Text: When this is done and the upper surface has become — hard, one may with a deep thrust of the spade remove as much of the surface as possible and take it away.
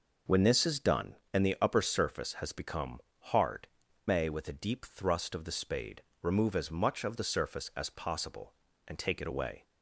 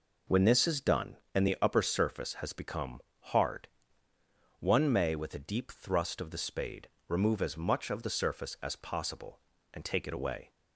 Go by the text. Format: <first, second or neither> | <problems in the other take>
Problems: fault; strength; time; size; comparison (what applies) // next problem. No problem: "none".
second | skips "one"; at 3.8 s // pauses between "spade" and "remove"; slight; at 6.0 s; 0.18 s long; slight in the second